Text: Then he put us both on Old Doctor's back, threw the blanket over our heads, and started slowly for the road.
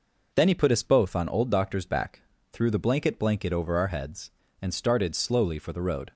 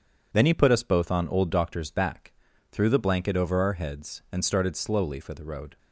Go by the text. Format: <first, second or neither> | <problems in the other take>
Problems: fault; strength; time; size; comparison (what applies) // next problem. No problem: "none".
second | says "blanket" twice; at 3.1 s